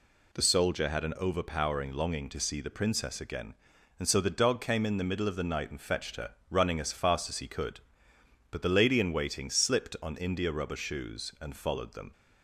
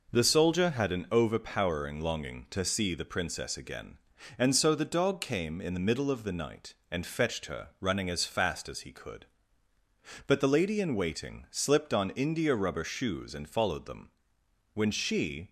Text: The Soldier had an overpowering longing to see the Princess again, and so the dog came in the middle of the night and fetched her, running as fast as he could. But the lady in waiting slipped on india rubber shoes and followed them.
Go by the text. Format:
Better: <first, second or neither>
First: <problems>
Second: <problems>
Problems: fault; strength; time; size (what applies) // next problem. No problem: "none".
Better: first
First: none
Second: goes on to say "When she"; noticeable; from 14.7 s on; 0.76 s long